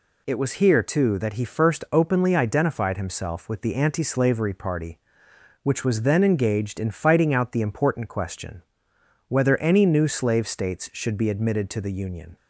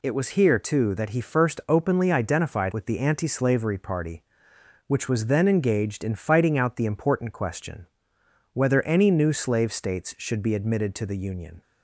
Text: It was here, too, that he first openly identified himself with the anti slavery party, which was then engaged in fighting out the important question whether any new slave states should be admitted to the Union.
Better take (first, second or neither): first